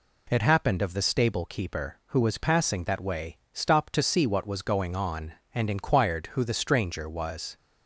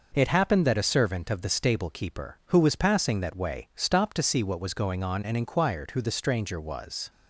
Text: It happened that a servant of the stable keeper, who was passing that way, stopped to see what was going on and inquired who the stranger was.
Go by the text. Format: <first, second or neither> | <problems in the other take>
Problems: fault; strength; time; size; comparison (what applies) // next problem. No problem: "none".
second | skips "that a servant"; at 0.8 s